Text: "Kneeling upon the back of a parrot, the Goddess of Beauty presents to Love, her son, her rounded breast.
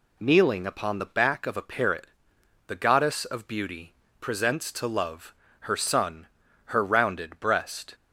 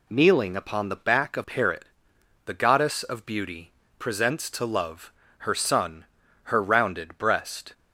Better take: first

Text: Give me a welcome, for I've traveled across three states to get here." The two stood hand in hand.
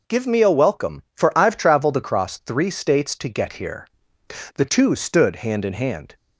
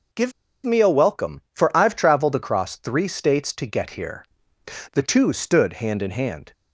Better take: first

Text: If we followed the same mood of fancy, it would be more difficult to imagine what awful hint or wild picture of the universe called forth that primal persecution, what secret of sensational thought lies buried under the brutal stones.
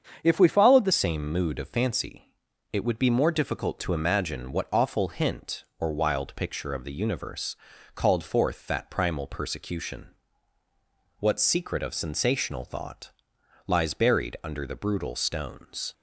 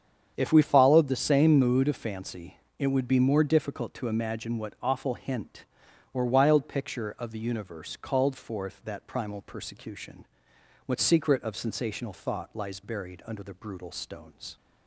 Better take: second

